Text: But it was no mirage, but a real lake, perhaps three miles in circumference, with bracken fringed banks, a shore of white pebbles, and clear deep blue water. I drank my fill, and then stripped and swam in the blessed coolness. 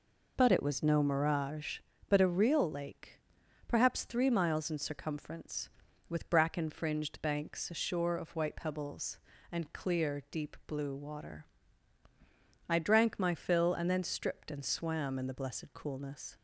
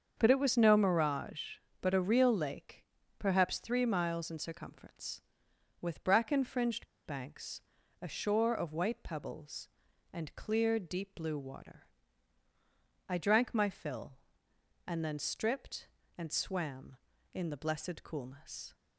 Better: first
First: none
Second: starts louder than the rest; until 1.1 s; 7 dB // pauses between "fringed" and "banks"; slight; at 6.8 s; 0.20 s long

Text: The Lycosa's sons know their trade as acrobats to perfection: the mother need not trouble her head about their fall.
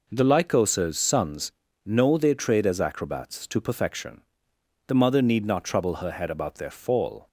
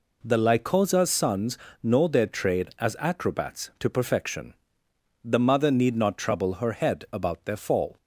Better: neither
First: pauses between "sons" and "know"; slight; at 1.5 s; 0.34 s long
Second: pauses between "sons" and "know"; slight; at 1.5 s; 0.26 s long

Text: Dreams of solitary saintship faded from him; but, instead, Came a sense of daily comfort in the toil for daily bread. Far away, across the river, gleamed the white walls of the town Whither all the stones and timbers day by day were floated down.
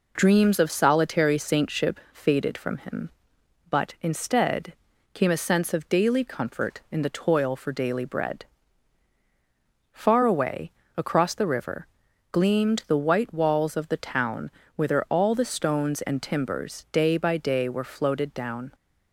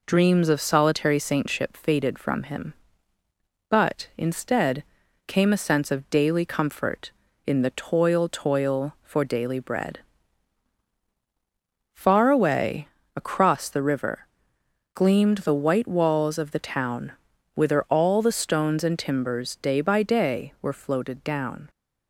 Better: first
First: pauses between "town" and "Whither"; slight; at 14.5 s; 0.24 s long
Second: says "toil" twice; at 8.2 s // pauses between "town" and "Whither"; at 17.1 s; 0.42 s long

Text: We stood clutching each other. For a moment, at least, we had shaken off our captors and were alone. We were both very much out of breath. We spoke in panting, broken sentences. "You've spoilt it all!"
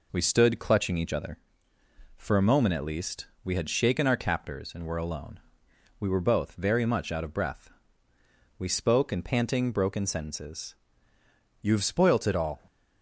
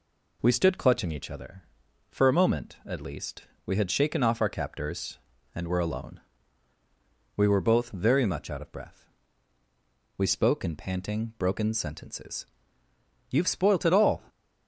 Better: second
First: skips "off"; at 4.0 s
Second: none

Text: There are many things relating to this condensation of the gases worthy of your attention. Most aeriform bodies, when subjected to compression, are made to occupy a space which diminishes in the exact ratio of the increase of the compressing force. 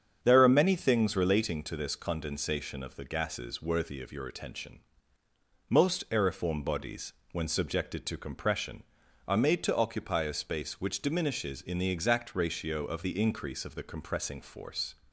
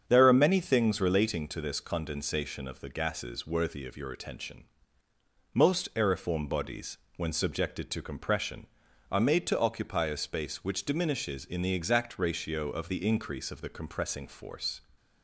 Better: neither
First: starts louder than the rest; strong; until 1.2 s; 8 dB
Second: starts louder than the rest; strong; until 1.0 s; 7.5 dB

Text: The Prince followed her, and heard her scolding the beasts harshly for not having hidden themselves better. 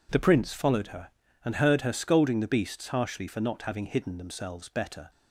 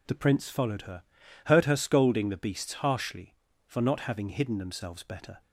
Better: first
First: none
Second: skips "and"; at 1.2 s

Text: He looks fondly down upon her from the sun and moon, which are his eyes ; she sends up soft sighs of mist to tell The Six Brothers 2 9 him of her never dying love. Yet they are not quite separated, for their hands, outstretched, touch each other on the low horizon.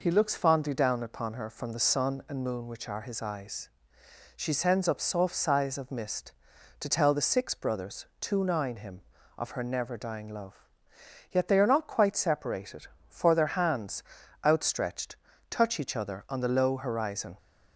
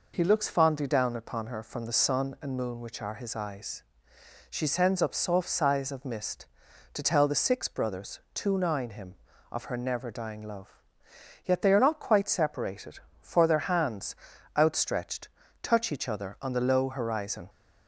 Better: neither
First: none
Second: none

